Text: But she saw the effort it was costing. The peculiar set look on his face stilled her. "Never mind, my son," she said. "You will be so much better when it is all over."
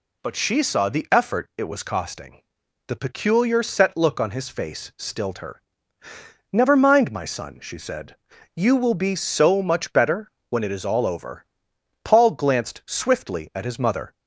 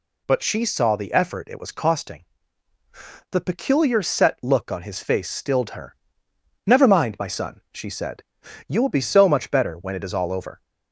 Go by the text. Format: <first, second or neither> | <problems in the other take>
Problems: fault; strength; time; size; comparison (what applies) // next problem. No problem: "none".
second | pauses between "better" and "when"; slight; at 10.2 s; 0.20 s long // goes on to say "Paul glanced swiftly at his mother"; strong; from 12.0 s on; 2.1 s long